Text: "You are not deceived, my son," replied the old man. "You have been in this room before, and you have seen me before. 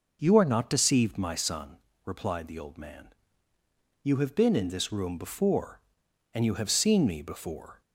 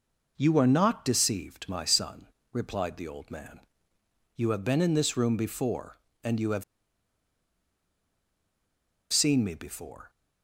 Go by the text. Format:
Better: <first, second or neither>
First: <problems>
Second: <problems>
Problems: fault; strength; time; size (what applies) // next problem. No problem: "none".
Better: first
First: none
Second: pauses between "have" and "seen"; strong; at 6.6 s; 2.4 s long